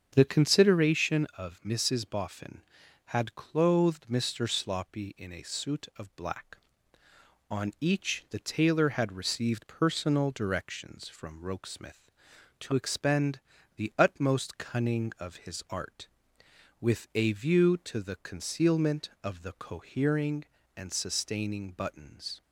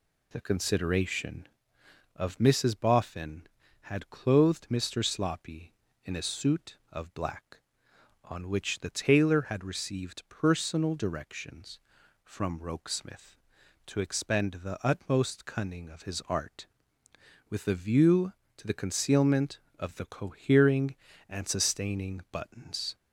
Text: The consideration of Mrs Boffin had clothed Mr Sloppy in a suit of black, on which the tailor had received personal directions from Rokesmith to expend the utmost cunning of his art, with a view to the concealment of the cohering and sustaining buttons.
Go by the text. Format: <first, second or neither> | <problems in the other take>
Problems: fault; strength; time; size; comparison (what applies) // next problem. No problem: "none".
second | starts louder than the rest; strong; until 1.1 s; 7.5 dB // says "each" for "which"; at 7.7 s // pauses between "expend" and "the"; at 13.3 s; 0.38 s long